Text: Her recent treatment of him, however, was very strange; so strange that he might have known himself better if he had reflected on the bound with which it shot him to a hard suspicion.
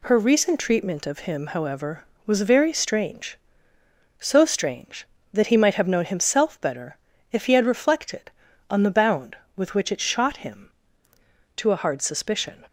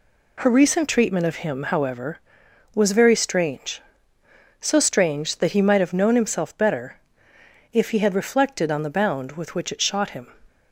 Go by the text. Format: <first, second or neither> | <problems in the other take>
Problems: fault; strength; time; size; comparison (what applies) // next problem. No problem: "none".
first | pauses between "better" and "if"; noticeable; at 6.9 s; 0.78 s long; slight in the first // stops before "to a hard suspicion"; at 10.4 s